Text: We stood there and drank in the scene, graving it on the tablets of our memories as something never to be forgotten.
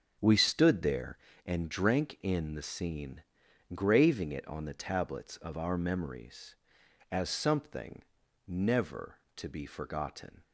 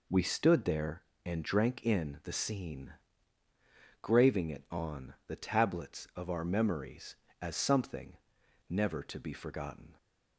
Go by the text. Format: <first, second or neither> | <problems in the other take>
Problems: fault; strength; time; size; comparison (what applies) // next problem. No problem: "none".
second | starts louder than the rest; strong; until 1.5 s; 7.5 dB // pauses between "something" and "never"; at 8.0 s; 0.44 s long; noticeable in the second